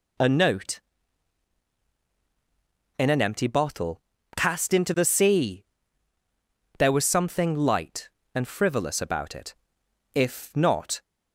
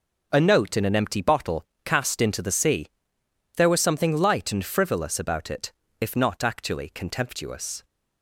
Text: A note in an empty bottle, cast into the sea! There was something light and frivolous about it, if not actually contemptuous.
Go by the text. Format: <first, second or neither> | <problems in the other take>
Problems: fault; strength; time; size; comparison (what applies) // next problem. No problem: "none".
second | stops before "actually contemptuous"; at 11.0 s